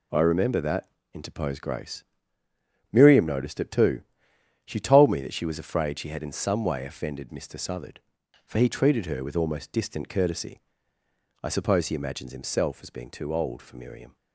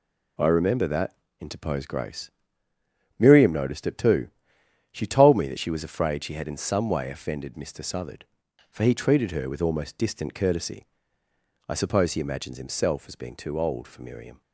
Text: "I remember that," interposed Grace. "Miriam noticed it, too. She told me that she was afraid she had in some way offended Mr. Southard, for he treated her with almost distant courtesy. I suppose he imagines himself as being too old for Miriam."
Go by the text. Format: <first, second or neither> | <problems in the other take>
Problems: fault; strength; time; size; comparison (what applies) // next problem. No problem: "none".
neither | none